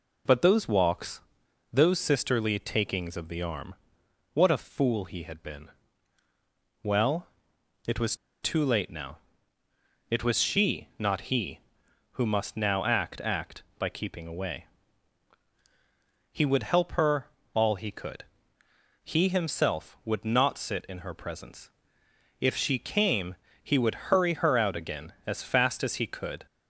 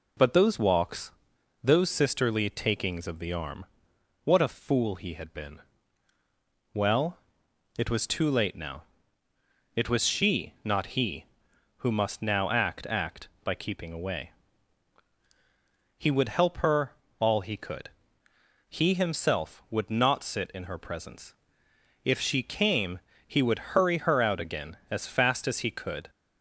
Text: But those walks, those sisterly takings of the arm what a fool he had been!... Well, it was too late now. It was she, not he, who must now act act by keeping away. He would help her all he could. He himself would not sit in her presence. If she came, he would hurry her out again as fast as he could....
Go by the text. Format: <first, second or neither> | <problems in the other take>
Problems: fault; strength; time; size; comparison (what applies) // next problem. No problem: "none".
second | pauses between "arm" and "what"; noticeable; at 3.7 s; 0.58 s long; noticeable in the second // pauses between "was" and "too"; slight; at 8.1 s; 0.28 s long // pauses between "her" and "all"; slight; at 17.2 s; 0.30 s long; slight in the second